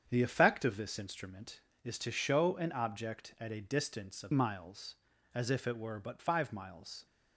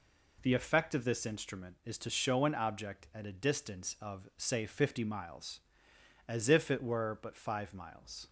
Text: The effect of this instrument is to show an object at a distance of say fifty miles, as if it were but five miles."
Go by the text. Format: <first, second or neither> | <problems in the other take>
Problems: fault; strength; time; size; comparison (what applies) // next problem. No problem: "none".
second | starts louder than the rest; strong; until 1.1 s; 7.5 dB // skips "say fifty"; at 4.3 s